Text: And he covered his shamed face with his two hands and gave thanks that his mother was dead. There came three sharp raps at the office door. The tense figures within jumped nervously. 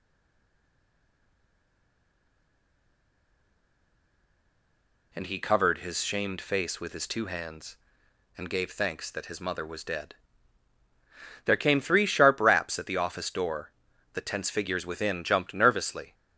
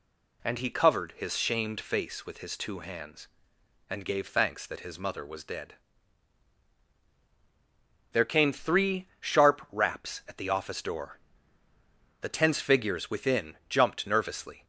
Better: second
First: stays silent before the first word; strong; until 5.1 s; 5.1 s long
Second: none

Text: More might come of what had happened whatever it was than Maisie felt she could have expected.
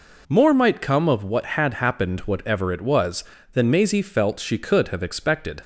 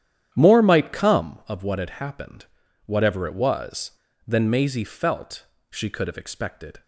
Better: first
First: none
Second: starts louder than the rest; strong; until 1.3 s; 10 dB // pauses between "happened" and "whatever"; at 2.4 s; 0.40 s long // pauses between "felt" and "she"; slight; at 5.4 s; 0.24 s long

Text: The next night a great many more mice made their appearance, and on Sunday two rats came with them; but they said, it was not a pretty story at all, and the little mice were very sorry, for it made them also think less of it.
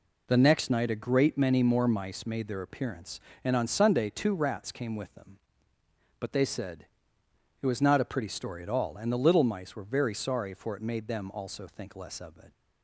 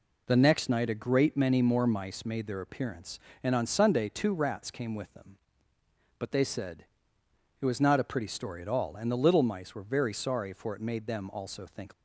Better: first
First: none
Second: stops before "less of it"; at 11.9 s

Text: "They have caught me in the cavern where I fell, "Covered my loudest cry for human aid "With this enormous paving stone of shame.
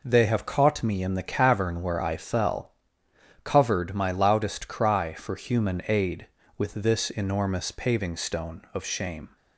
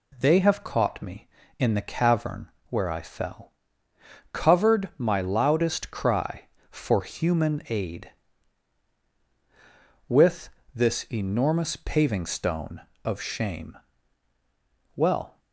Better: first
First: none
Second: pauses between "cavern" and "where"; slight; at 2.5 s; 0.18 s long // pauses between "With" and "this"; slight; at 10.4 s; 0.26 s long // goes on to say "Well"; slight; from 14.9 s on; 0.44 s long

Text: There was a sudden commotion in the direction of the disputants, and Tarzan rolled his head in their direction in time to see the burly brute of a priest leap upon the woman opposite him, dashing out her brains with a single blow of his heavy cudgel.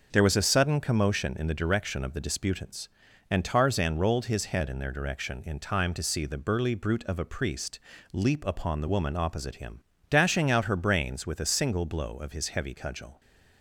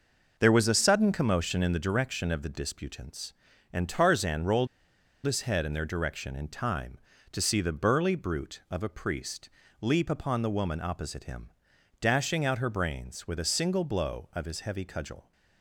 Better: first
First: pauses between "priest" and "leap"; slight; at 7.7 s; 0.34 s long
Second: pauses between "rolled" and "his"; noticeable; at 4.6 s; 0.58 s long // pauses between "priest" and "leap"; slight; at 9.4 s; 0.32 s long

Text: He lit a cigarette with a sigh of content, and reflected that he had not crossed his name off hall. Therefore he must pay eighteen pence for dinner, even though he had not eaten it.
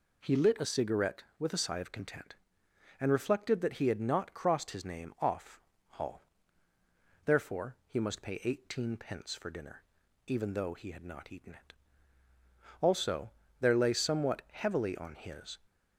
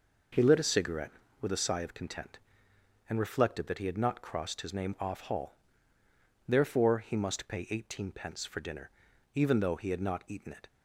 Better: second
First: pauses between "off" and "hall"; slight; at 5.5 s; 0.30 s long // goes on to say "Also there lay somewhat heavily on his"; strong; from 12.8 s on; 2.7 s long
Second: none

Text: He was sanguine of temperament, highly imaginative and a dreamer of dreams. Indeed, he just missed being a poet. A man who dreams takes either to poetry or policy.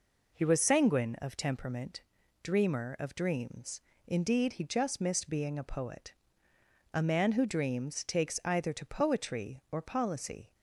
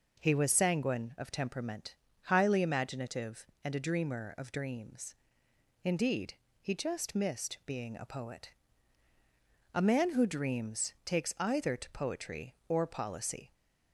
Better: second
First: skips "highly imaginative and a"; at 2.2 s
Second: none

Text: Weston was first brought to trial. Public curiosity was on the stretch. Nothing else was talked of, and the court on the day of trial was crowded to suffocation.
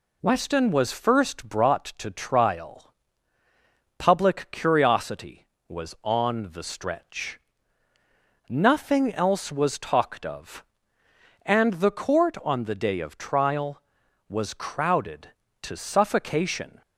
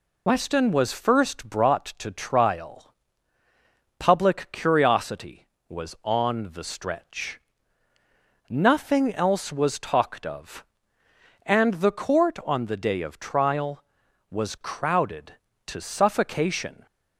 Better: first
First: none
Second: loses the start of "Weston"; at 0.2 s; 35 ms

